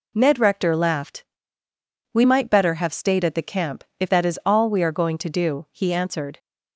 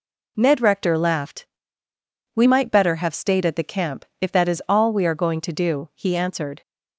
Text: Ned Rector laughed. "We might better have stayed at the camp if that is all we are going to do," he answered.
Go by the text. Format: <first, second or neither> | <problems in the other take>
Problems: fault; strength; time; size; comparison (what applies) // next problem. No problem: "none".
neither | pauses between "camp" and "if"; slight; the same in both